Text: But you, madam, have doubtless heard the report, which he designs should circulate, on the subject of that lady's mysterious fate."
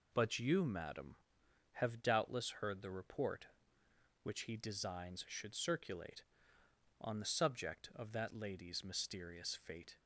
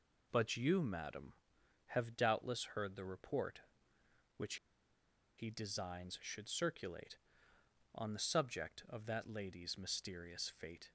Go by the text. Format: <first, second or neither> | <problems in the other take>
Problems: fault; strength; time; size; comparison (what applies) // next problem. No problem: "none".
first | pauses between "which" and "he"; noticeable; at 4.5 s; 0.82 s long